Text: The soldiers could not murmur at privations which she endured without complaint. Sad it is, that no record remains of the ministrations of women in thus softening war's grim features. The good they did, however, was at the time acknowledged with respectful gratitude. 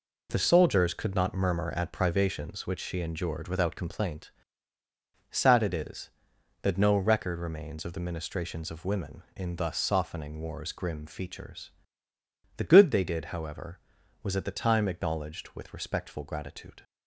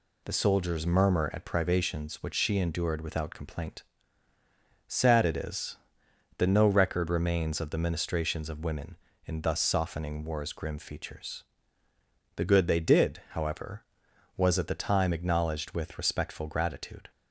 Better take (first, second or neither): first